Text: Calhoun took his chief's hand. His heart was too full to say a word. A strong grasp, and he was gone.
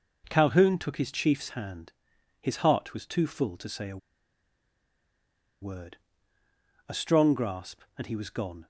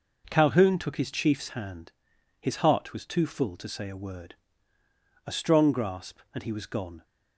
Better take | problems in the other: second | pauses between "a" and "word"; strong; at 3.9 s; 1.6 s long

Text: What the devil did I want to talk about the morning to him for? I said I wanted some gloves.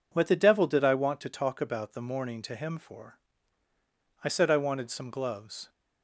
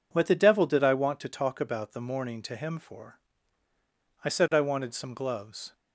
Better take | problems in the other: neither | none

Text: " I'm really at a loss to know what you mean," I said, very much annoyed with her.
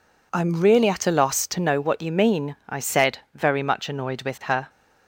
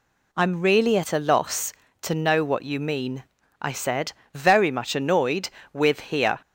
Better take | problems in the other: first | says "here" for "her"; at 6.0 s

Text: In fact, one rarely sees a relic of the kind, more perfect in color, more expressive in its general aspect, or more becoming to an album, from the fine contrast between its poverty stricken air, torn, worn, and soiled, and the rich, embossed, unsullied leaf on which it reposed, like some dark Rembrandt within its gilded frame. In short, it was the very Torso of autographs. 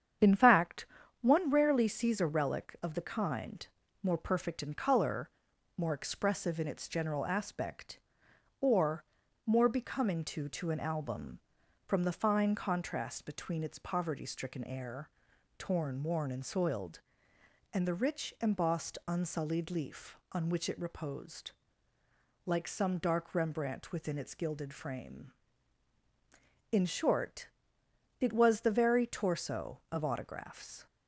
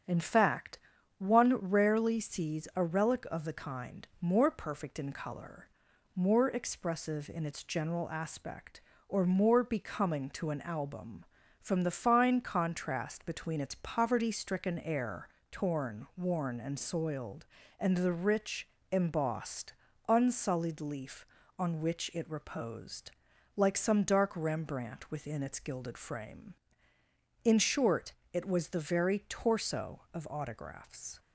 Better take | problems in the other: second | starts louder than the rest; strong; until 1.5 s; 8.5 dB; strong in the second // pauses between "or" and "more"; at 9.0 s; 0.42 s long // says "to" twice; at 10.4 s

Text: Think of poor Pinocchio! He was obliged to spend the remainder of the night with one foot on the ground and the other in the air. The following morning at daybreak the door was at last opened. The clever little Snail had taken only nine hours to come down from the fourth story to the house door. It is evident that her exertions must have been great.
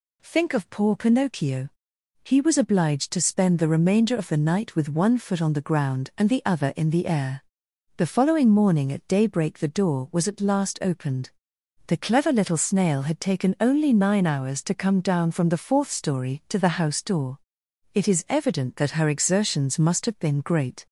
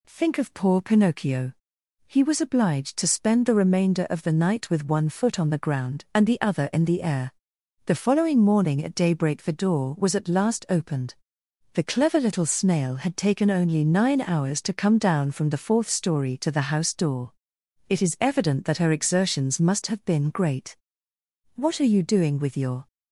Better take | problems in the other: first | goes on to say "What are you doing with your"; from 21.5 s on; 1.3 s long

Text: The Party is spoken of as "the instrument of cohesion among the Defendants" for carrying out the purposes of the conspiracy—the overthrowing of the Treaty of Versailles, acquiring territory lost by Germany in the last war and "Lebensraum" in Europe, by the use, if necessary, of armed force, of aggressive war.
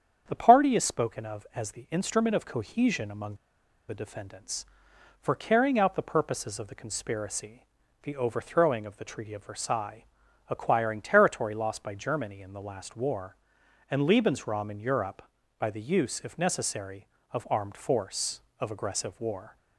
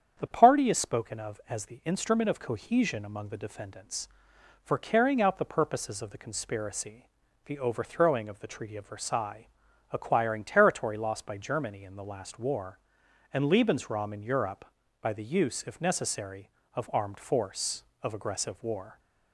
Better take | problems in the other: second | starts louder than the rest; strong; until 1.2 s; 8 dB; strong in the second // pauses between "among" and "the"; noticeable; at 3.3 s; 0.53 s long

